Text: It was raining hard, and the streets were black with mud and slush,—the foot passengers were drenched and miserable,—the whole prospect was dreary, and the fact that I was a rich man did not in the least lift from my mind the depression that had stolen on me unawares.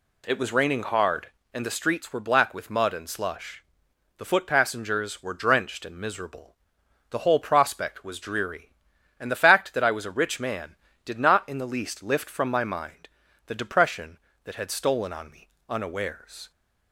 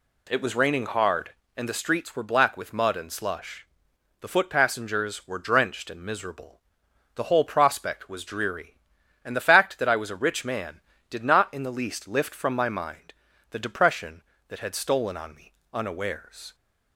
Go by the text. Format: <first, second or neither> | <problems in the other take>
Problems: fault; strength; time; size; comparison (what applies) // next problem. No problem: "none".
neither | pauses between "mind" and "the"; the same in both // pauses between "me" and "unawares"; slight; the same in both